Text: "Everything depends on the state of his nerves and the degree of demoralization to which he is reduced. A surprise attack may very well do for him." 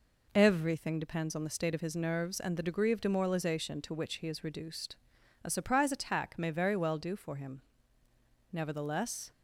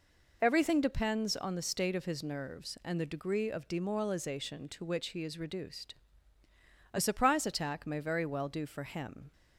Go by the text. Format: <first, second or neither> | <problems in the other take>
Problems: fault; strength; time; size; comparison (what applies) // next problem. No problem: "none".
second | goes on to say "Nevertheless"; noticeable; from 8.5 s on; 0.78 s long